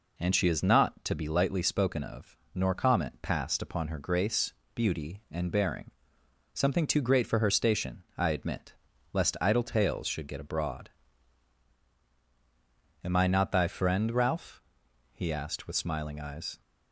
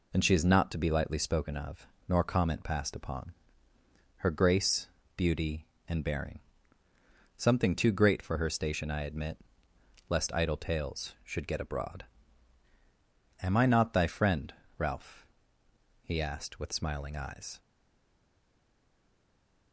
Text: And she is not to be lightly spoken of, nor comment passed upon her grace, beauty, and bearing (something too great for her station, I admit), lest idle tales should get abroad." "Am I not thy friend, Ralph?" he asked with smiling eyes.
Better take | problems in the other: first | pauses between "upon" and "her"; noticeable; at 3.3 s; 0.84 s long // stays silent after the last word; from 17.5 s on; 2.2 s long

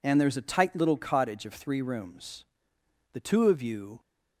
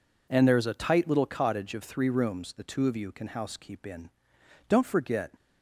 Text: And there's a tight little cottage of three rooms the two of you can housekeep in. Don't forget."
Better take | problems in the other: second | pauses between "rooms" and "the"; noticeable; at 2.4 s; 0.70 s long // stops before "can housekeep in Don't forget"; at 3.9 s

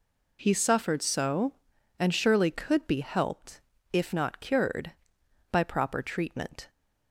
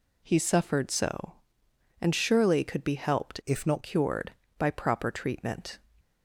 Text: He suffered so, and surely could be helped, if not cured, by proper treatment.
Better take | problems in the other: first | changes voice from "if" to "not"; from 3.4 to 3.8 s; 0.4 s long

